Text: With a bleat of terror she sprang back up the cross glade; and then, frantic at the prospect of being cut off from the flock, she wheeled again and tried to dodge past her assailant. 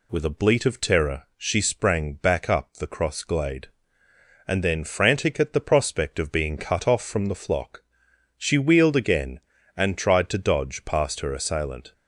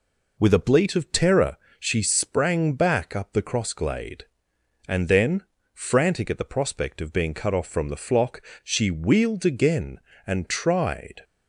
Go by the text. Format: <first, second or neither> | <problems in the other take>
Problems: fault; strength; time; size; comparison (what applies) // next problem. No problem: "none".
first | pauses between "terror" and "she"; slight; at 1.5 s; 0.22 s long // stops before "to dodge past her assailant"; at 11.2 s